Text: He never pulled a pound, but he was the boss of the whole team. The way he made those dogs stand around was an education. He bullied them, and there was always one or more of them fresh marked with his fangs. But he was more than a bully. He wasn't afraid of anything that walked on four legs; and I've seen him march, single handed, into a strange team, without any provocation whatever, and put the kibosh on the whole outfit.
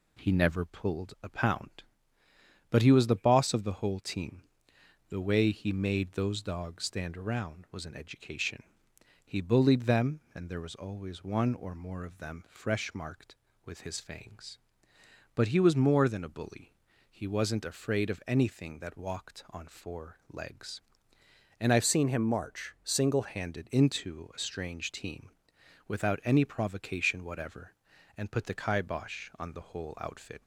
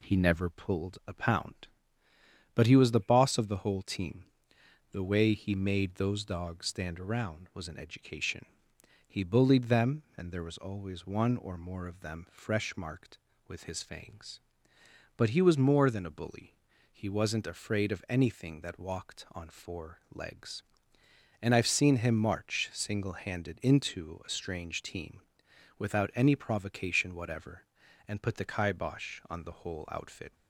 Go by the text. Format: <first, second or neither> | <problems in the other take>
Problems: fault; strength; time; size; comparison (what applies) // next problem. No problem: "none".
second | changes voice from "seen" to "single"; from 21.8 to 23.2 s; 1.4 s long